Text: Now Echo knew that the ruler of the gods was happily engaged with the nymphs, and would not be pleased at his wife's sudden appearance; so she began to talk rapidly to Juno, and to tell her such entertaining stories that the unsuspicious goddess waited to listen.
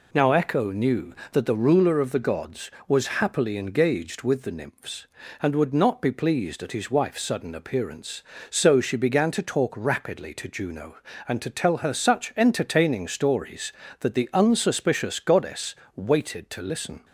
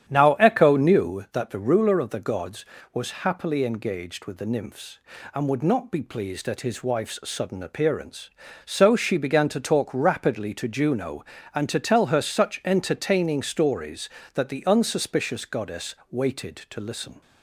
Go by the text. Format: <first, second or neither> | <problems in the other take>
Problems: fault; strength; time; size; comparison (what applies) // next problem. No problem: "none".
first | starts louder than the rest; strong; until 1.3 s; 9.5 dB // pauses between "goddess" and "waited"; slight; at 15.9 s; 0.16 s long; slight in the first